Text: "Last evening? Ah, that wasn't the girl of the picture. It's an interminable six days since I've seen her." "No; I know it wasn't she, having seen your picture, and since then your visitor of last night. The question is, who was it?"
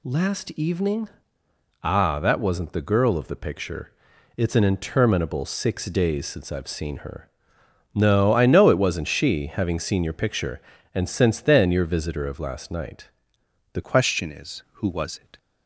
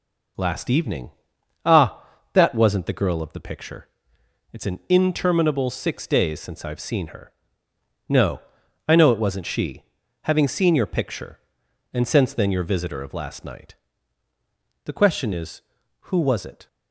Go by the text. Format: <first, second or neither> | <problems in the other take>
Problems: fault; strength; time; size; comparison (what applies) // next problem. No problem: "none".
second | changes voice at "question"; from 13.8 s on; 1.5 s long